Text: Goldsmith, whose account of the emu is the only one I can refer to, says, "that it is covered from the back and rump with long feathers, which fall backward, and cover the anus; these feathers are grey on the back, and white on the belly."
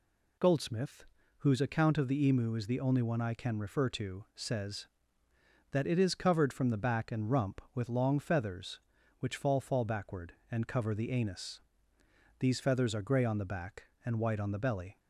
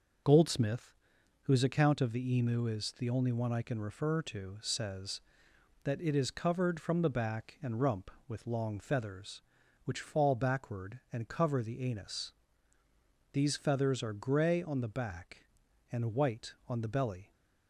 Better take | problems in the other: second | says "fall" twice; at 9.5 s

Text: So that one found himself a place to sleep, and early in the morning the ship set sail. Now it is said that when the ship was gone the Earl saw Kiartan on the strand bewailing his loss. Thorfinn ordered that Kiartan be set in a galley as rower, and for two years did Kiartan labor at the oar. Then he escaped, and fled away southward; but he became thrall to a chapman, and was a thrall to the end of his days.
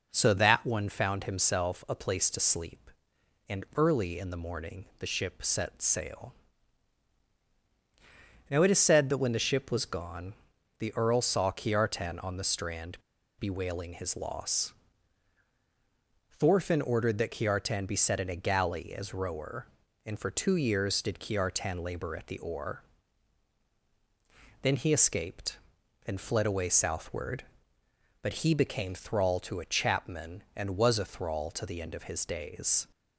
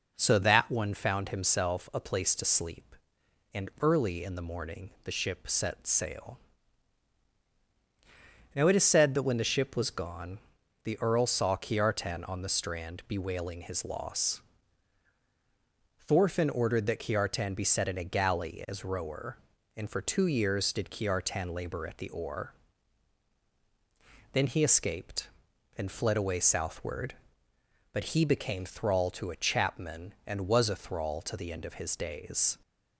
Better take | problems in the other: second | pauses between "gone" and "the"; noticeable; at 10.3 s; 0.46 s long; noticeable in the second // pauses between "strand" and "bewailing"; at 12.9 s; 0.39 s long

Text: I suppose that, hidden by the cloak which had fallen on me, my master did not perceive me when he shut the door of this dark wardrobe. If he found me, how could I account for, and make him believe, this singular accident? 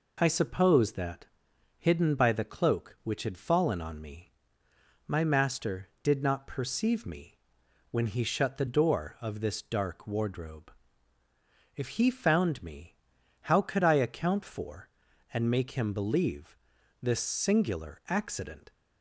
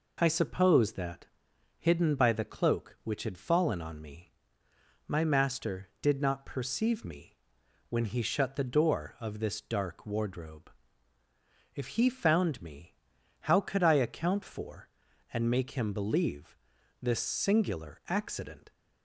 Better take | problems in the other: neither | pauses between "me" and "when"; noticeable; the same in both

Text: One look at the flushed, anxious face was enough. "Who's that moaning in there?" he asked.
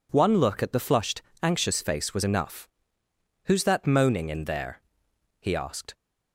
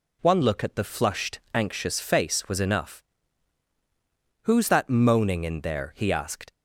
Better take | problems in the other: neither | none

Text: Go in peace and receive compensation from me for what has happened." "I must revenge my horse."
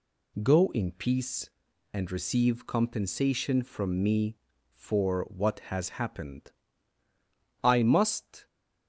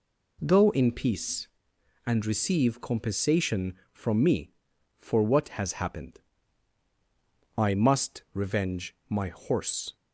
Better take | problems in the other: second | stops before "revenge my horse"; at 8.4 s

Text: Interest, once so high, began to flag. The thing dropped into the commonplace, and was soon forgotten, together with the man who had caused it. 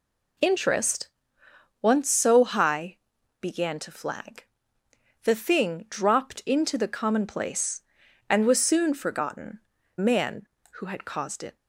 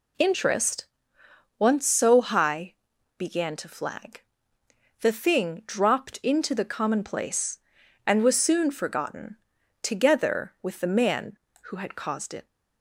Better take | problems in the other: second | skips "together with the"; at 9.7 s

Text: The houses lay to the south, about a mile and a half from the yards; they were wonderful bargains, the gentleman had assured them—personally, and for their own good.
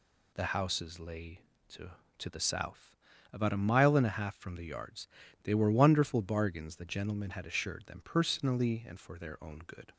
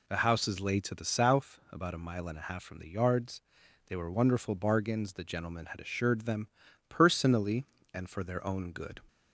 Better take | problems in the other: second | says "to" twice; at 2.1 s

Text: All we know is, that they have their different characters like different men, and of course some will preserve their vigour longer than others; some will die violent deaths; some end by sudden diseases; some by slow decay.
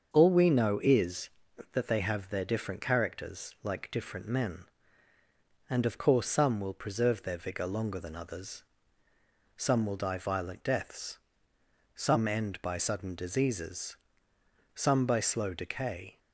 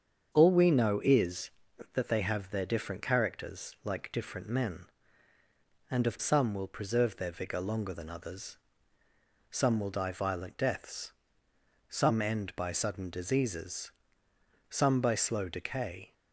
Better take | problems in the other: first | starts louder than the rest; strong; until 1.3 s; 7 dB; also in the first // skips "course"; at 6.1 s

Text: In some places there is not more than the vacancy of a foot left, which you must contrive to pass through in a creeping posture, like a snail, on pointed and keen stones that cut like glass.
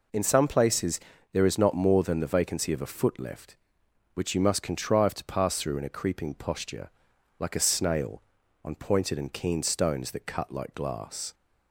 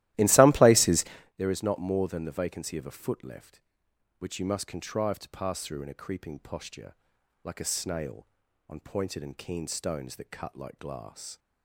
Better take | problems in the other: first | starts louder than the rest; strong; until 1.3 s; 15.5 dB // pauses between "places" and "there"; slight; at 1.0 s; 0.32 s long; slight in the first

